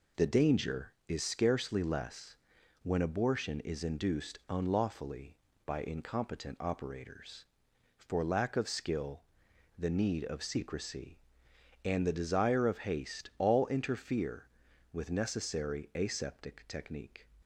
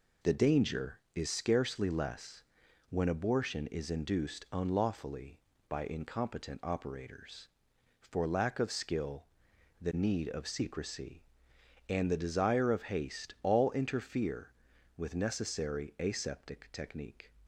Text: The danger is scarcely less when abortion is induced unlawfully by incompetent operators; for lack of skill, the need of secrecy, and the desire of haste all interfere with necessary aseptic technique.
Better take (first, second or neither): neither